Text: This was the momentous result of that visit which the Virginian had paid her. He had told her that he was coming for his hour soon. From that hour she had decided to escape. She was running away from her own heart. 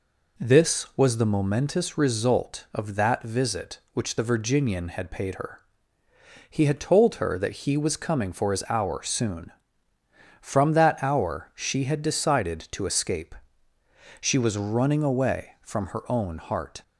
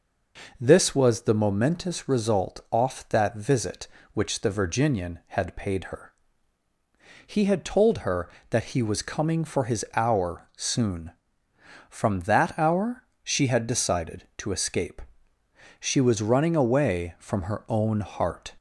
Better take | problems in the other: first | says "off" for "of"; at 2.7 s // pauses between "hour" and "she"; slight; at 13.0 s; 0.18 s long

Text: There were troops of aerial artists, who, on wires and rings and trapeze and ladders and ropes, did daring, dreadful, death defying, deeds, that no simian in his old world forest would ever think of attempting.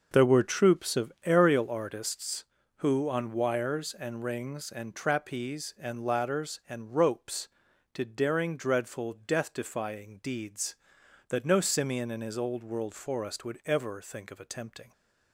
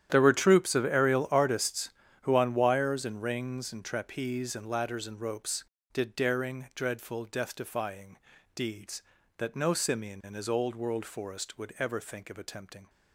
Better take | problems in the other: first | gets quieter; strong; throughout; 16 dB

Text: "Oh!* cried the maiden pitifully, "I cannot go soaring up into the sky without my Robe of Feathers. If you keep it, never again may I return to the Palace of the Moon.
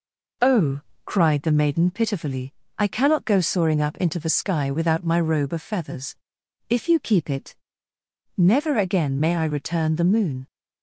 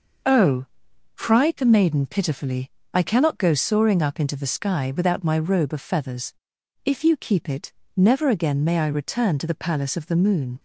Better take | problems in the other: second | skips "to the Palace of"; at 9.9 s

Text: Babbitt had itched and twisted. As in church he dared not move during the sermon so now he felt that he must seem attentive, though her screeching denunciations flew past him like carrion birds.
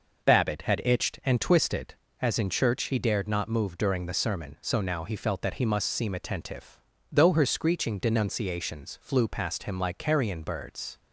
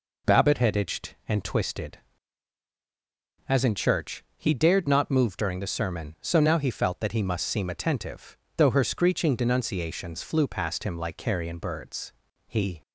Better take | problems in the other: first | goes on to say "He"; slight; from 12.4 s on; 0.34 s long

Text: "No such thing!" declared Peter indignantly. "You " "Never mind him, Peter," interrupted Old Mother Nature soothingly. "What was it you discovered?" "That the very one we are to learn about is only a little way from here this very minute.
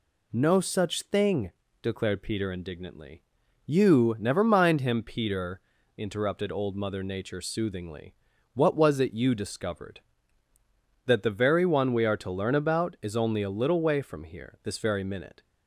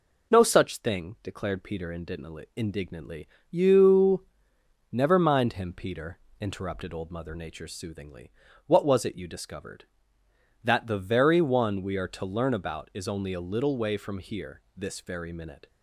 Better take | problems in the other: first | says "indignantly" twice; at 2.5 s

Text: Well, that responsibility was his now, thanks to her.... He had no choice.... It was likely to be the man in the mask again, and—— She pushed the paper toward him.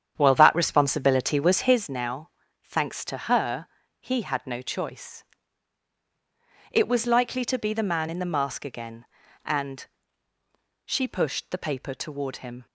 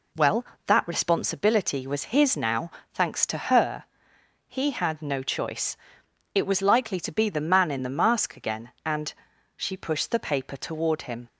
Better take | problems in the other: second | starts louder than the rest; strong; until 1.8 s; 9 dB

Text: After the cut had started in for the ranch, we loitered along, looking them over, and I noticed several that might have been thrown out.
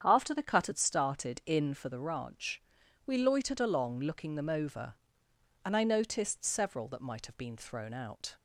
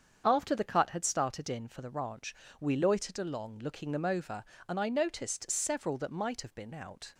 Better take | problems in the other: first | starts louder than the rest; strong; until 1.2 s; 7 dB; strong in the first // skips "thrown"; at 6.7 s

